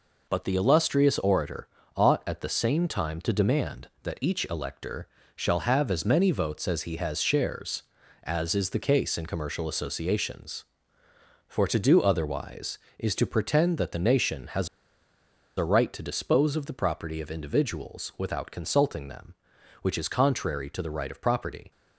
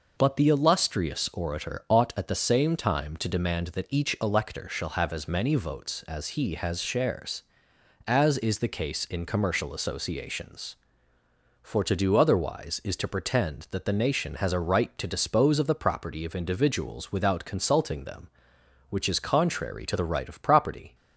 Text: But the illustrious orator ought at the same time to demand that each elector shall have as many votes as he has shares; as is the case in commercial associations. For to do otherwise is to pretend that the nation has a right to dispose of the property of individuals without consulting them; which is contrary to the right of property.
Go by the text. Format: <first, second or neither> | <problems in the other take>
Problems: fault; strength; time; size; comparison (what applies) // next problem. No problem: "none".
second | pauses between "orator" and "ought"; slight; at 1.6 s; 0.28 s long // pauses between "elector" and "shall"; slight; at 5.0 s; 0.28 s long // pauses between "has" and "a"; noticeable; at 14.6 s; 0.89 s long